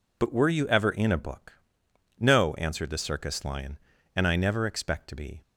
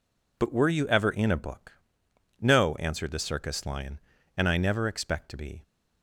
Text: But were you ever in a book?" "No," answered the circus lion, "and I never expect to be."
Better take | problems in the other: neither | none

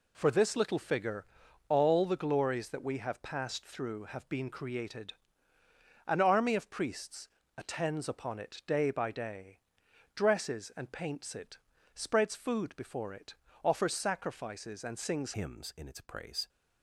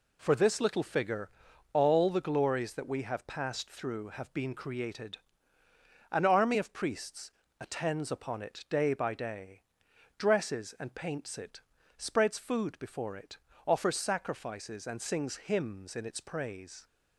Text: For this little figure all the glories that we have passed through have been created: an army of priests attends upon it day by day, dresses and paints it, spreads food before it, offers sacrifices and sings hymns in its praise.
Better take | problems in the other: second | pauses between "figure" and "all"; at 1.2 s; 0.42 s long; also in the second // pauses between "priests" and "attends"; slight; at 7.2 s; 0.30 s long; slight in the second // changes voice at "hymns"; from 15.3 s on; 1.1 s long

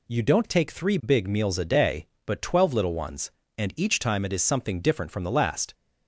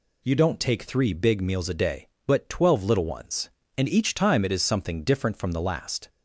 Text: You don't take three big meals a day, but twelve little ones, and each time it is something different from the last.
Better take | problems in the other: neither | none

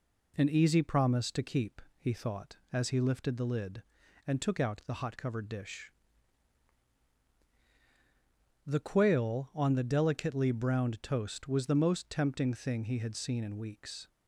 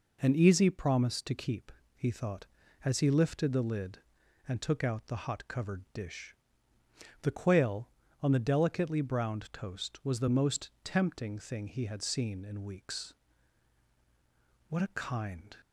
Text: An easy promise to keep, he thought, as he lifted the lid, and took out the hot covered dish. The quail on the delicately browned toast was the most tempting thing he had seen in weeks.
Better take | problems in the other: first | goes on to say "What a kind"; noticeable; from 14.6 s on; 0.86 s long

